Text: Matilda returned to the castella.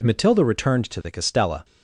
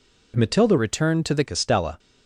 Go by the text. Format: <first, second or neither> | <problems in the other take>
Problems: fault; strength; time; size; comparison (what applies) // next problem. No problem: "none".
first | changes voice from "returned" to "the"; from 0.7 to 1.4 s; 0.7 s long